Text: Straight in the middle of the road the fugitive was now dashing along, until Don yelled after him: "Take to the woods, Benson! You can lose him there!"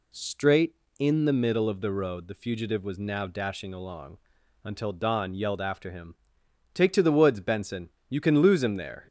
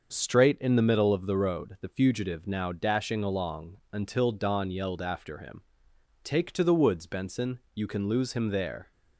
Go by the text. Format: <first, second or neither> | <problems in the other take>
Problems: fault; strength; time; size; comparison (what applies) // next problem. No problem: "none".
first | starts louder than the rest; until 1.1 s; 6.5 dB // skips "was"; at 2.4 s